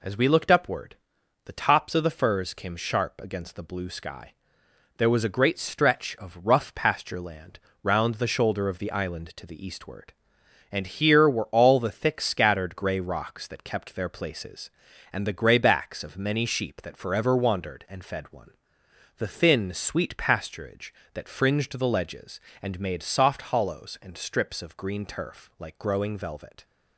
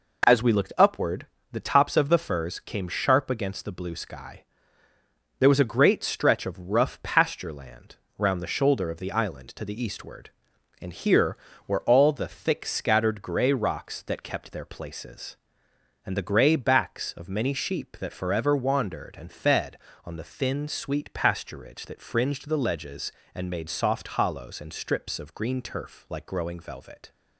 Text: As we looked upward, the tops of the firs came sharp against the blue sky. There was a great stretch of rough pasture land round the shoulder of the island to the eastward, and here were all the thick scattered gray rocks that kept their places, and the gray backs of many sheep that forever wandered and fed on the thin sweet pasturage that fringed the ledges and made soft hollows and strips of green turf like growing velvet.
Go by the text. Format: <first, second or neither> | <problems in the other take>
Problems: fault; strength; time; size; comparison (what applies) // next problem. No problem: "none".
second | pauses between "land" and "round"; slight; at 7.5 s; 0.24 s long; slight in the second // says "one" for "on"; at 18.3 s